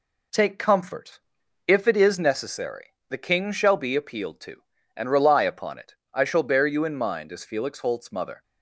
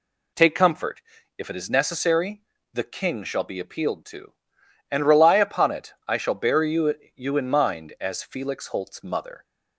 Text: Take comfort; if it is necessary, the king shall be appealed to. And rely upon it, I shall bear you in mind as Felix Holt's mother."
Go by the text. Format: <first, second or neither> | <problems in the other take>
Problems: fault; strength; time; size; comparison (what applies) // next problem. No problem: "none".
first | says "you" twice; at 7.1 s